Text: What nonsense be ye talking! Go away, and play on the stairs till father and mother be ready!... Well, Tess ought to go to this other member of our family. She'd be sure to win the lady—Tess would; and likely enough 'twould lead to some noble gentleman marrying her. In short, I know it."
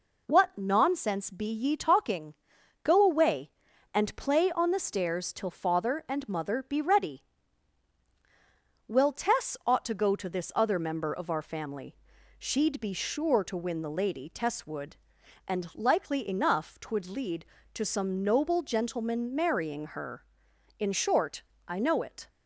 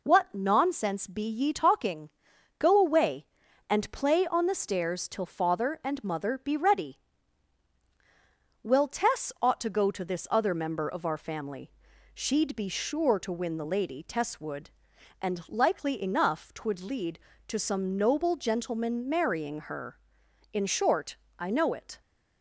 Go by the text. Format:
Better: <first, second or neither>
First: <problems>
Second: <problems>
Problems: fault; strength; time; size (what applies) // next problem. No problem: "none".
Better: neither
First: none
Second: none